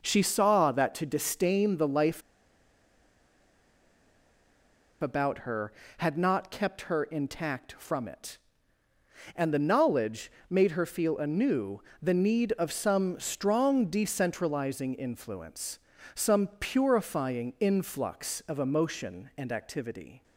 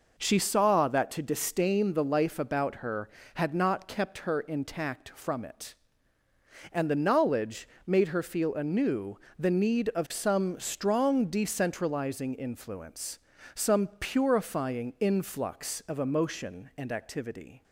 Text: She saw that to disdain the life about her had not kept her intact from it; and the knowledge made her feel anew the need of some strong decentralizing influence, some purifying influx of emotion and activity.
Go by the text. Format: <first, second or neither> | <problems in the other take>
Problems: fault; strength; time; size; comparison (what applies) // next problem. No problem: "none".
second | pauses between "life" and "about"; strong; at 2.2 s; 2.8 s long // pauses between "knowledge" and "made"; slight; at 10.3 s; 0.18 s long; slight in the second // pauses between "anew" and "the"; slight; at 11.8 s; 0.18 s long; slight in the second